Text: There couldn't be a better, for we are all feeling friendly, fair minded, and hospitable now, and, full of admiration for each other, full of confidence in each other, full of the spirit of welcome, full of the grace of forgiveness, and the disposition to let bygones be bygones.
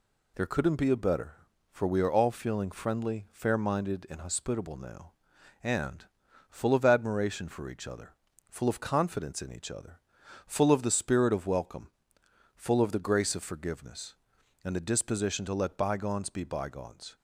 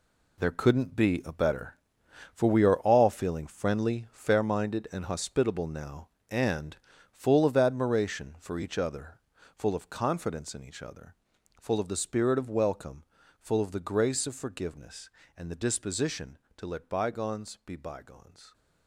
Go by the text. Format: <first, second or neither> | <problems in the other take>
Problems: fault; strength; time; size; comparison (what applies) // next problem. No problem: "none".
first | gets quieter; strong; throughout; 10 dB